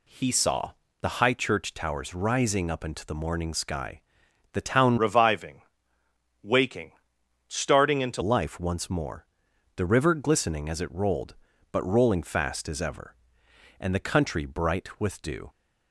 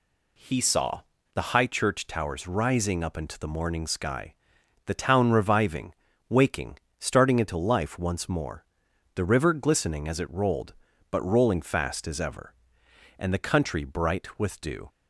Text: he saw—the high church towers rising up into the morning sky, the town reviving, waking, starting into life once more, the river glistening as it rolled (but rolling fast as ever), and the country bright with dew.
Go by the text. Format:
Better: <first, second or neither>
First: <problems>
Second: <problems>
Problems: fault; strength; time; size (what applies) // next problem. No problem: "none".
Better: second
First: changes voice from "reviving" to "into"; from 4.9 to 8.2 s; 3.3 s long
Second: none